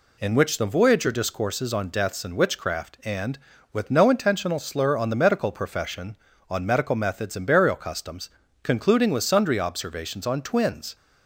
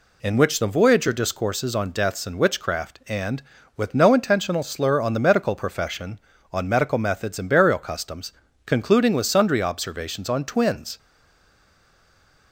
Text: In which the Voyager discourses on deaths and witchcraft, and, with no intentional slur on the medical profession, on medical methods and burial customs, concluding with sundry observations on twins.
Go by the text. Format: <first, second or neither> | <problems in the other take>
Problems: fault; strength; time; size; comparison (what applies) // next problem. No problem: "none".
first | stays silent after the last word; noticeable; from 10.9 s on; 1.6 s long